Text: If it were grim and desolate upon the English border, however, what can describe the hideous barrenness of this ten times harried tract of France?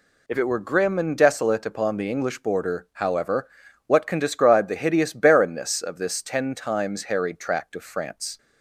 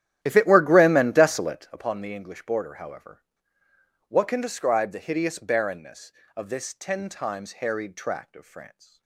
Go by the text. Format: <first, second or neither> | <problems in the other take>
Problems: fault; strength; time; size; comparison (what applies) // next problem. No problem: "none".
first | starts louder than the rest; strong; until 1.7 s; 11.5 dB